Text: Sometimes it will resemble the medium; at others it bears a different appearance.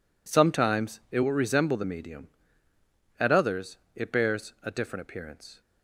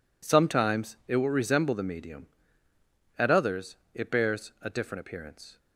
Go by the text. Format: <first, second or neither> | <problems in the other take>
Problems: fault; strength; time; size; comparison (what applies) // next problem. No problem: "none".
neither | pauses between "others" and "it"; slight; the same in both